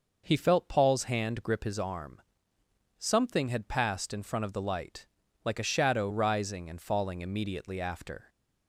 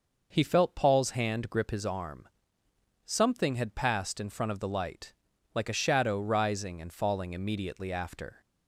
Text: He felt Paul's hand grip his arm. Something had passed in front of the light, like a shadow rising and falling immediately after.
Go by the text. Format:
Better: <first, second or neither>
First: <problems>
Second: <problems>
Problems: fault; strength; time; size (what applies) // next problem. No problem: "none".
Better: neither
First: none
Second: none